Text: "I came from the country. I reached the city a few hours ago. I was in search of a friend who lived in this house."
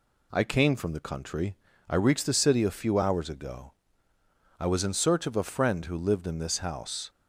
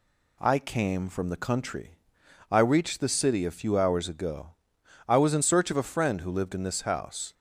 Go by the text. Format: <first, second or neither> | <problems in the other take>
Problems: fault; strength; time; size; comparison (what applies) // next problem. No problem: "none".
neither | none